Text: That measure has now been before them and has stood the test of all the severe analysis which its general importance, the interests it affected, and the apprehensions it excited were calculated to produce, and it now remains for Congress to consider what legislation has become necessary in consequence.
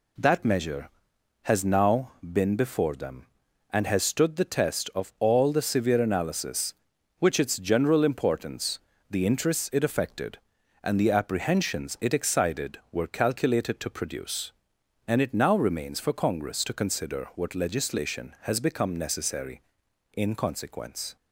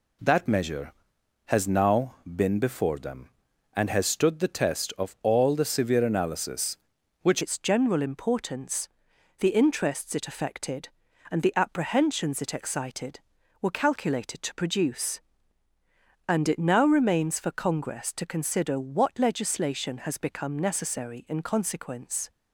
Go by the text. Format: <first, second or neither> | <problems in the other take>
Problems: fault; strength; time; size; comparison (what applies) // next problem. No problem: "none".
first | changes voice at "its"; from 7.4 s on; 14.8 s long